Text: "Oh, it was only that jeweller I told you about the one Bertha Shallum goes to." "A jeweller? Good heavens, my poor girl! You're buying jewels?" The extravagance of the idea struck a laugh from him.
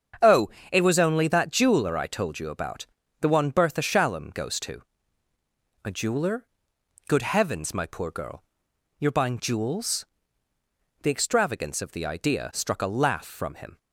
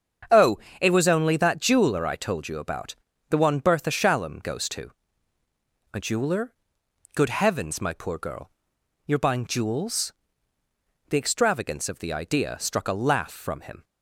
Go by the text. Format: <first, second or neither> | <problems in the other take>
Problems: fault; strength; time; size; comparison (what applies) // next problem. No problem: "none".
neither | starts louder than the rest; strong; the same in both // pauses between "about" and "the"; slight; the same in both